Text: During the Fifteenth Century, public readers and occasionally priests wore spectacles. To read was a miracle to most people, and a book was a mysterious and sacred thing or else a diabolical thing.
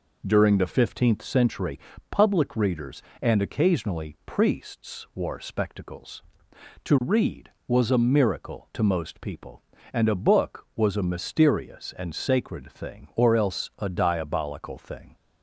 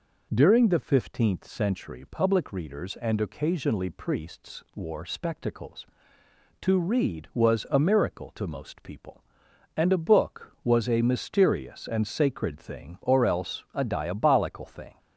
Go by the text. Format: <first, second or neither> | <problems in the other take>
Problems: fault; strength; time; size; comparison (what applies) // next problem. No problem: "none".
neither | none